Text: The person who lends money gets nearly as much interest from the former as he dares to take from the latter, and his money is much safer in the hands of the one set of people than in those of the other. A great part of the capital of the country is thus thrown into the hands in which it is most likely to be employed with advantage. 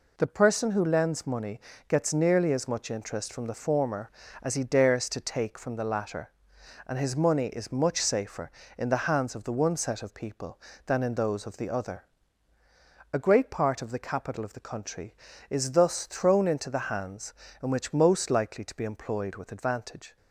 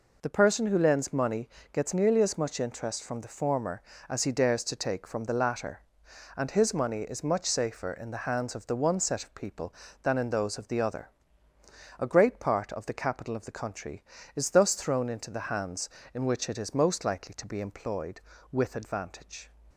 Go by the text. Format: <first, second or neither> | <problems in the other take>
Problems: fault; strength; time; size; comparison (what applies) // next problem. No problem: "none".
second | pauses between "money" and "gets"; slight; at 1.5 s; 0.28 s long; slight in the second // skips "it is"; at 17.9 s